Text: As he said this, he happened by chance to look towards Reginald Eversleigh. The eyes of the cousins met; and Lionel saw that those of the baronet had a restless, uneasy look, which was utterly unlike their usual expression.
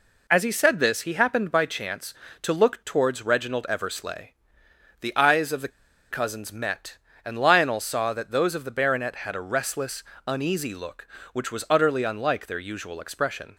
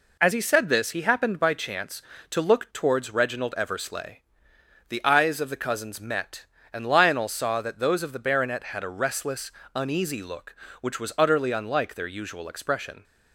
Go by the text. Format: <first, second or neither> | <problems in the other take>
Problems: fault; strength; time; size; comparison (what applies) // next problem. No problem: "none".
second | pauses between "the" and "cousins"; at 5.7 s; 0.40 s long